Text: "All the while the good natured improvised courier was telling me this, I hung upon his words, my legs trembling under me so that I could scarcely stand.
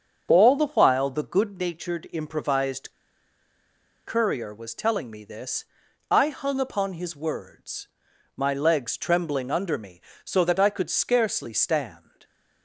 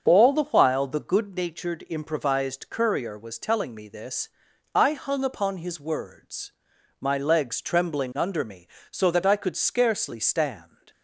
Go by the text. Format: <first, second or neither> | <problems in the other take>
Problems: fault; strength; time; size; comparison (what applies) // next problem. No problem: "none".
second | starts louder than the rest; until 1.3 s; 6.5 dB; also in the second // pauses between "improvised" and "courier"; at 2.9 s; 1.1 s long